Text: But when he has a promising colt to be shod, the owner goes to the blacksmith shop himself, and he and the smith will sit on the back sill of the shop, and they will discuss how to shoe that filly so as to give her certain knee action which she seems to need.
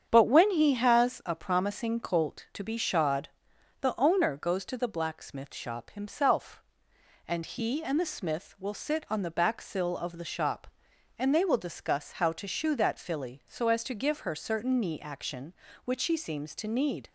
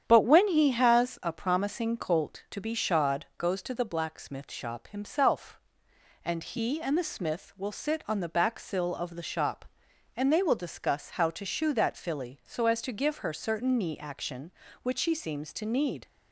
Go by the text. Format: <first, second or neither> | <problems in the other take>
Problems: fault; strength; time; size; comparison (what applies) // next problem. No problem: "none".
first | starts louder than the rest; strong; until 1.0 s; 9 dB; strong in the first // skips "the owner"; at 3.3 s